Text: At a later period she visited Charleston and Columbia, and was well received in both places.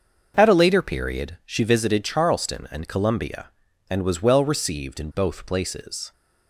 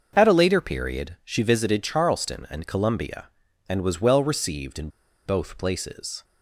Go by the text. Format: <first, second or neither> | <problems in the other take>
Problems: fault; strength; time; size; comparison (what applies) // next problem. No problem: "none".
first | starts louder than the rest; until 1.1 s; 6.5 dB; also in the first // pauses between "in" and "both"; at 4.8 s; 0.37 s long